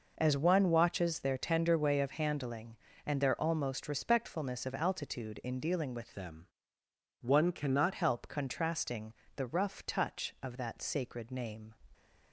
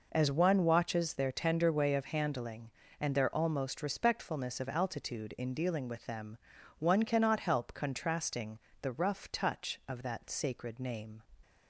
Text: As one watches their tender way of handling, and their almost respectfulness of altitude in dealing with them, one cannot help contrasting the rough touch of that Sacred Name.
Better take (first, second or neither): second